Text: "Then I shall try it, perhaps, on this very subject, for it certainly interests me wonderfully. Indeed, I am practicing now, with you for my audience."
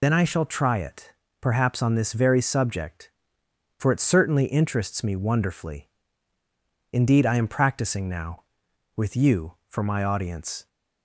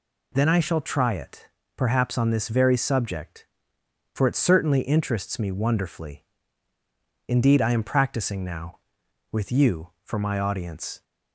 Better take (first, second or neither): second